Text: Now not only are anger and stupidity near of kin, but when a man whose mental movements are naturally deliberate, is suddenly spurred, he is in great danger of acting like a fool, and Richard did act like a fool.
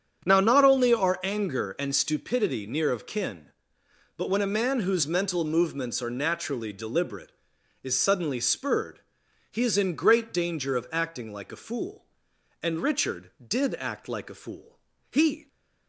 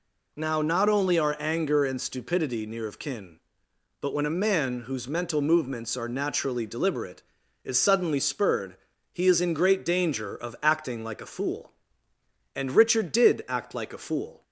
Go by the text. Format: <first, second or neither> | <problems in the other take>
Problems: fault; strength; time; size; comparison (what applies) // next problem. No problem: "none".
second | starts louder than the rest; strong; until 1.2 s; 8.5 dB // goes on to say "He"; slight; from 15.1 s on; 0.36 s long